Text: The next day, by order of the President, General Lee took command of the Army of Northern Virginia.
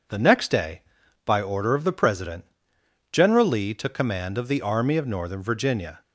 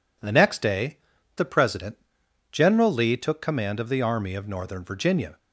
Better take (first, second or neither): first